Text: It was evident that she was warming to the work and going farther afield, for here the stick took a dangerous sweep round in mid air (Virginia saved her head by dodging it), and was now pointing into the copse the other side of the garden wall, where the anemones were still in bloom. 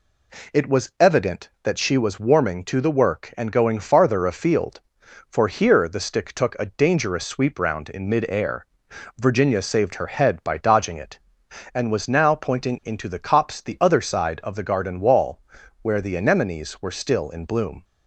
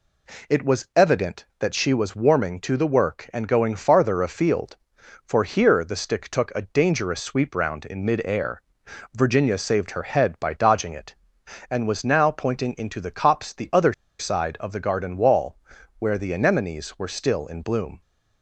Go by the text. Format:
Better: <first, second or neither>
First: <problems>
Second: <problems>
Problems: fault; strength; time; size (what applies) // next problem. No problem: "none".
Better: first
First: none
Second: pauses between "other" and "side"; slight; at 13.9 s; 0.25 s long